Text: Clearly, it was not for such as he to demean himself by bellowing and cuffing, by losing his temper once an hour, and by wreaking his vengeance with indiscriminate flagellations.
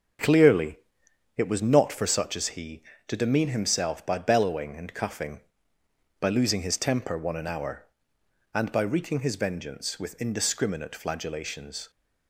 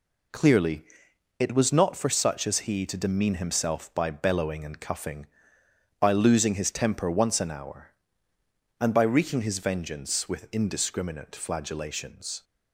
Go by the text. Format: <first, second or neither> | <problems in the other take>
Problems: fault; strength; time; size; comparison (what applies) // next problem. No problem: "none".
second | starts louder than the rest; until 1.7 s; 6.5 dB // says "one" for "once"; at 7.1 s